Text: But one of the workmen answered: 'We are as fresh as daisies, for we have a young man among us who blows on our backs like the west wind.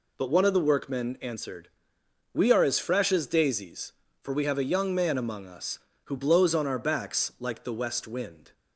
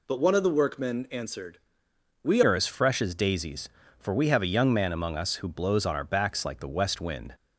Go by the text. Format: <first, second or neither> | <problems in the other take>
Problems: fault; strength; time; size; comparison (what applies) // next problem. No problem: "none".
first | changes voice at "are"; from 2.4 s on; 4.9 s long